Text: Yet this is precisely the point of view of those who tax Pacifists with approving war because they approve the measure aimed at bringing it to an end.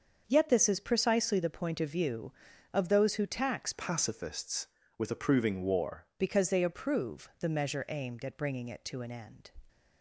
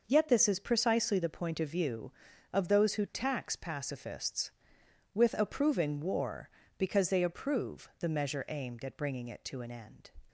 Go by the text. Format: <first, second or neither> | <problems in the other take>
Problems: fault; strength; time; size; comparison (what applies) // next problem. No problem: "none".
second | starts louder than the rest; until 1.2 s; 6.5 dB // changes voice from "Pacifists" to "war"; from 3.7 to 6.0 s; 2.3 s long